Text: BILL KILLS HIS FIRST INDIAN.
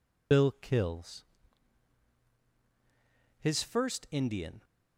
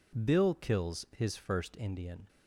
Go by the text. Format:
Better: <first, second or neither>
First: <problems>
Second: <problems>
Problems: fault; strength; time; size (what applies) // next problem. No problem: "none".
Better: second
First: loses the start of "BILL"; at 0.3 s; 50 ms // pauses between "KILLS" and "HIS"; strong; at 1.2 s; 2.1 s long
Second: none